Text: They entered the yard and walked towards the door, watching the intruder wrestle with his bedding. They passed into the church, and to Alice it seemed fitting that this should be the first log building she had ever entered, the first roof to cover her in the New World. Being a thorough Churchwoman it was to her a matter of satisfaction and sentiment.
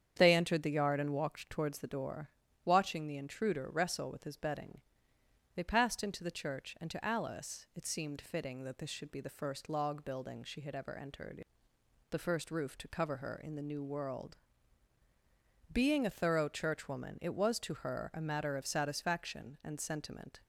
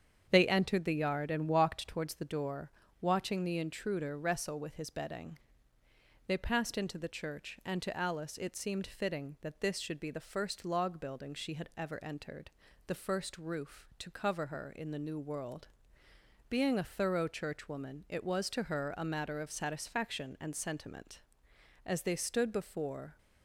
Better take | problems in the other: first | starts louder than the rest; strong; until 1.3 s; 8 dB; strong in the first // goes on to say "As they stood before"; from 21.8 s on; 1.3 s long

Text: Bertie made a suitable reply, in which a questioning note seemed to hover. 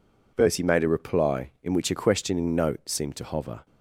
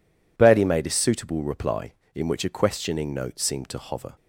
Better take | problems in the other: second | skips "suitable"; at 0.8 s

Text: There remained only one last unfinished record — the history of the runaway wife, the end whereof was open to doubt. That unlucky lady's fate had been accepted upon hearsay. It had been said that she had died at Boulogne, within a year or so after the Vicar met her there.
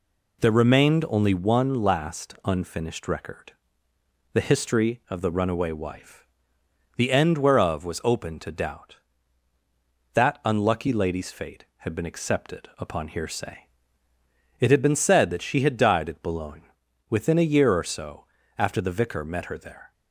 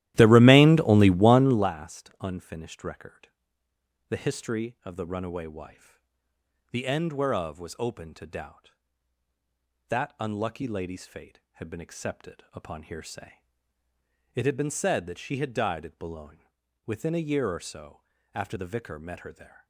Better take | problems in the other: first | starts louder than the rest; strong; until 1.7 s; 14.5 dB // pauses between "so" and "after"; slight; at 18.0 s; 0.34 s long; slight in the first

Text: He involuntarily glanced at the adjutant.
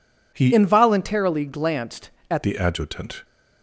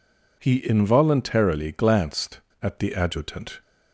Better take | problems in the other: second | changes voice from "involuntarily" to "at"; from 0.5 to 2.4 s; 1.9 s long

